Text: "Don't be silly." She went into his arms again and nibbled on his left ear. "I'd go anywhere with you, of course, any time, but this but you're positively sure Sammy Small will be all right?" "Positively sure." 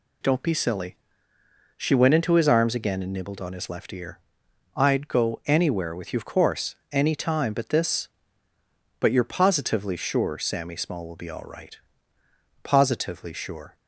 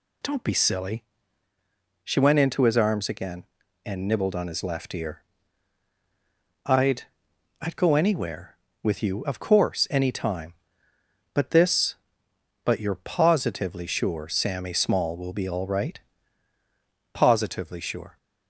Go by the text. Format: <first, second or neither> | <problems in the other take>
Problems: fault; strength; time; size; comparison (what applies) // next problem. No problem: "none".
first | says "I'd" twice; at 7.6 s